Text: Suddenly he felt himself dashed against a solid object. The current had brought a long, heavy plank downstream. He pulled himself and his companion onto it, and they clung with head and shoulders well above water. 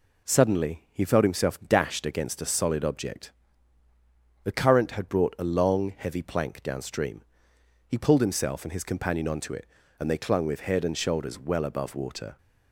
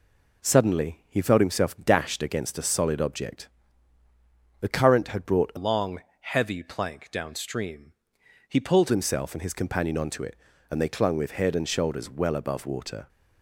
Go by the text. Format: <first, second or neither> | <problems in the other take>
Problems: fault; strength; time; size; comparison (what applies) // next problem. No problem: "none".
first | changes voice from "long" to "pulled"; from 5.5 to 8.9 s; 3.4 s long